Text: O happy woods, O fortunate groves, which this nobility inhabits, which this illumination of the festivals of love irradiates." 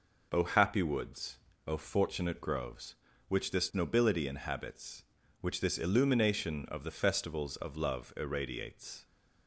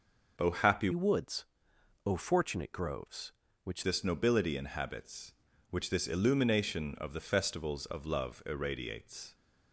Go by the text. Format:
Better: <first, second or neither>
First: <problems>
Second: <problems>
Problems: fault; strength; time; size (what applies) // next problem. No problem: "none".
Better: first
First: none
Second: changes voice from "woods" to "which"; from 0.9 to 3.8 s; 2.9 s long